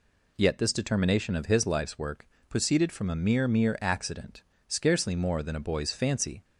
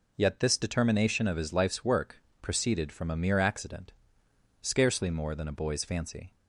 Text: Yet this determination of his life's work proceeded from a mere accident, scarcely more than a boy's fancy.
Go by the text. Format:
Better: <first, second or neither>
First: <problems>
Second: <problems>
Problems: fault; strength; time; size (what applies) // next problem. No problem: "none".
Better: second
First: pauses between "work" and "proceeded"; slight; at 2.2 s; 0.24 s long // says "mere" twice; at 3.4 s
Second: pauses between "work" and "proceeded"; slight; at 2.2 s; 0.20 s long